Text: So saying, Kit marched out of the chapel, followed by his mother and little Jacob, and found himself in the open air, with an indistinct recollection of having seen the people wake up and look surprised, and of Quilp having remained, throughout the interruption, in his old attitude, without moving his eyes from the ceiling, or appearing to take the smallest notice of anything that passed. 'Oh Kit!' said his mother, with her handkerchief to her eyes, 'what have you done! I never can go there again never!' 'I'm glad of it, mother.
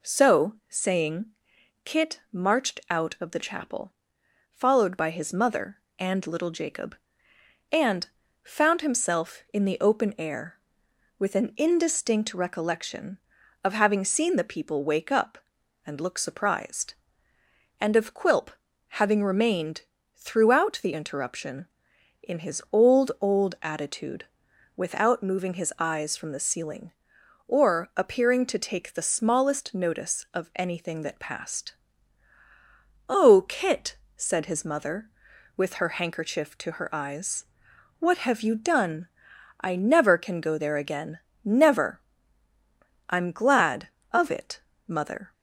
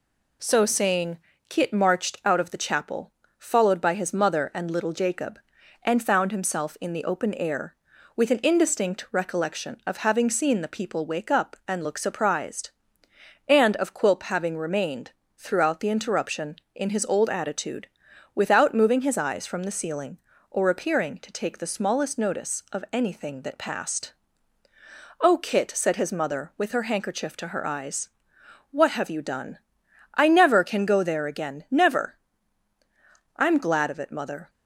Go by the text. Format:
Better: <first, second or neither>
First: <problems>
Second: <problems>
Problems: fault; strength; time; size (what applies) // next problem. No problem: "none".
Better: second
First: pauses between "and" and "found"; slight; at 8.0 s; 0.36 s long // pauses between "Quilp" and "having"; noticeable; at 18.4 s; 0.46 s long // says "old" twice; at 23.2 s // pauses between "again" and "never"; slight; at 41.2 s; 0.24 s long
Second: none